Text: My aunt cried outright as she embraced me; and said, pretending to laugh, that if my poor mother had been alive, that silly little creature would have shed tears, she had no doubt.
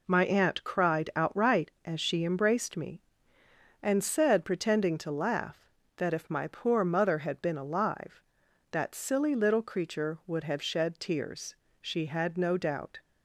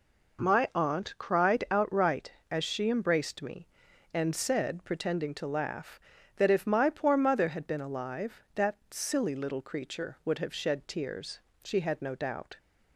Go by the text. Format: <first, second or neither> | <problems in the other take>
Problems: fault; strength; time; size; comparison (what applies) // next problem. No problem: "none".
neither | none